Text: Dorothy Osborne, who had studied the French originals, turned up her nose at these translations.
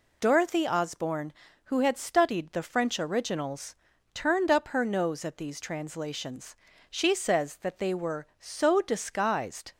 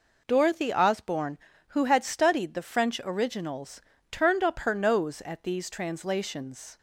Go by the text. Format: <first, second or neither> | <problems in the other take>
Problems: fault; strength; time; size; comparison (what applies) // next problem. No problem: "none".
second | goes on to say "She says that they were so disguised"; strong; from 6.8 s on; 2.8 s long